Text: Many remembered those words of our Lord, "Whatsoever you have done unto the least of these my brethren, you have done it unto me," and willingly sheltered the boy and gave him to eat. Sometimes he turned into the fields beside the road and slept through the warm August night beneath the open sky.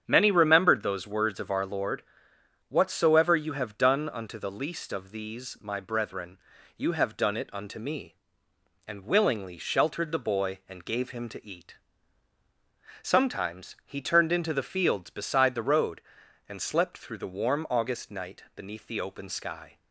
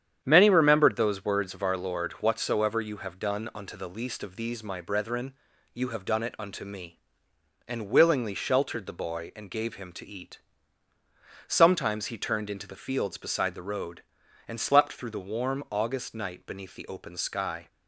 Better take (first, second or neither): neither